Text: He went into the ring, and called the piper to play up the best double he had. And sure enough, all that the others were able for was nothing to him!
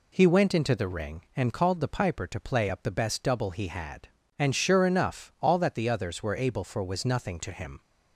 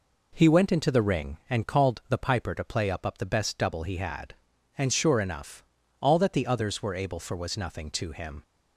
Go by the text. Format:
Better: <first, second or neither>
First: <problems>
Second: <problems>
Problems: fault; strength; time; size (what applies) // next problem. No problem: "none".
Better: first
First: none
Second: says "up" twice; at 3.0 s